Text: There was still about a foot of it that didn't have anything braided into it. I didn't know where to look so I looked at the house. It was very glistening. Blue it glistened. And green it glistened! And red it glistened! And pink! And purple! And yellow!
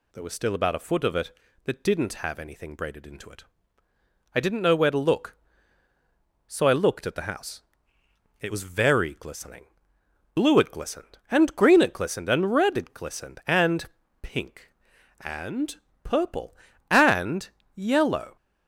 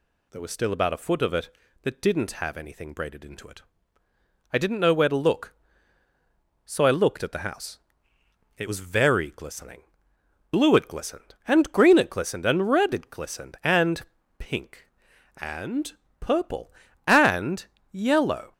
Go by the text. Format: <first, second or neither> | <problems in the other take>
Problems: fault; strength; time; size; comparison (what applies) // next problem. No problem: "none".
neither | pauses between "And" and "pink"; slight; the same in both // pauses between "And" and "purple"; slight; the same in both // pauses between "And" and "yellow"; slight; the same in both